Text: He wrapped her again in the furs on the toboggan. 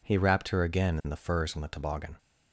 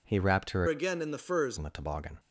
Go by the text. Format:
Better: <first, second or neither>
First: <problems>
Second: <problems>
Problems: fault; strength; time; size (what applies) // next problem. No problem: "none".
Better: first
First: none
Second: changes voice from "again" to "furs"; from 0.6 to 1.5 s; 0.9 s long